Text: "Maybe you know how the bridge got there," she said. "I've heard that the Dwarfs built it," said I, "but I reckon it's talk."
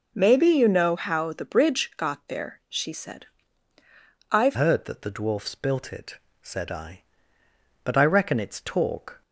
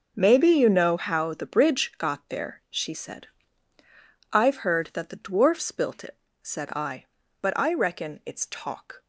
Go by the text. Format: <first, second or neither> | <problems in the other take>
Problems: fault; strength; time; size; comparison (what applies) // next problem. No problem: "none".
second | changes voice at "heard"; from 4.5 s on; 4.7 s long